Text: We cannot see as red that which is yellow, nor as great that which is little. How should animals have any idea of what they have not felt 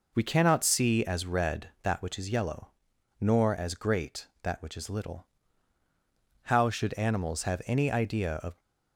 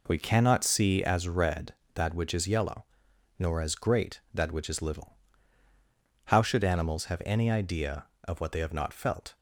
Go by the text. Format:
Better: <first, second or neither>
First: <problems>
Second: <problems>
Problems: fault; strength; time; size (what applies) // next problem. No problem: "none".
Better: second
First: stops before "what they have not felt"; at 8.5 s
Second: none